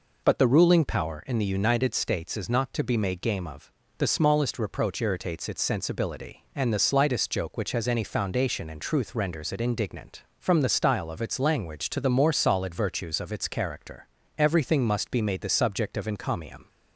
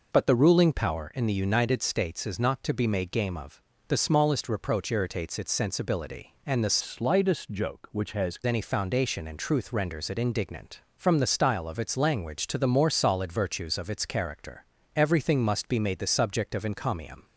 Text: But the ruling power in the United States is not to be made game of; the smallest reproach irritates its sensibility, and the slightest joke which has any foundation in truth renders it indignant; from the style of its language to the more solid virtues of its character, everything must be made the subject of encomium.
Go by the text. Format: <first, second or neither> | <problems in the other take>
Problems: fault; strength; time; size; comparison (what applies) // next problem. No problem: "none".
first | changes voice from "slightest" to "has"; from 6.7 to 8.3 s; 1.6 s long